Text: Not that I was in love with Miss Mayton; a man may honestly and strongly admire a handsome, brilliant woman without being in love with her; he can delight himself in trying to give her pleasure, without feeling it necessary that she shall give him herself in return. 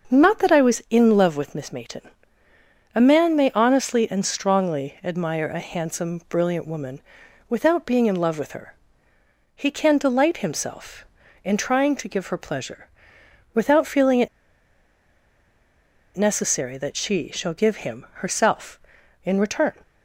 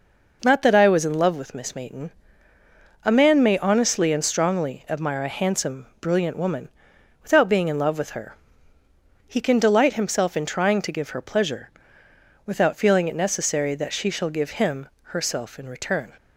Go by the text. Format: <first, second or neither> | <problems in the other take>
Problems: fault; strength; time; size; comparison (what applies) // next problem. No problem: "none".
second | starts louder than the rest; until 1.1 s; 6 dB // pauses between "woman" and "without"; noticeable; at 7.0 s; 0.48 s long; noticeable in the second // pauses between "it" and "necessary"; strong; at 14.2 s; 1.8 s long // pauses between "him" and "herself"; slight; at 18.0 s; 0.16 s long; slight in the second